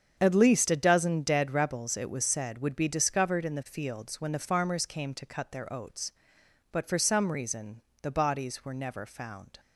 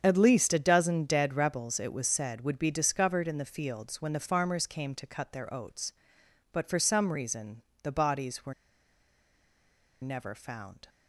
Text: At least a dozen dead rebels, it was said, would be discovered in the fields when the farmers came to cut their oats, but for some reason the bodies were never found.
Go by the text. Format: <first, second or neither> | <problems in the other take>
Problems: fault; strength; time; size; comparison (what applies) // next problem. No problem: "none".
first | starts louder than the rest; strong; until 1.0 s; 7.5 dB; strong in the first // pauses between "reason" and "the"; slight; at 7.6 s; 0.22 s long; slight in the first // pauses between "were" and "never"; strong; at 8.5 s; 1.4 s long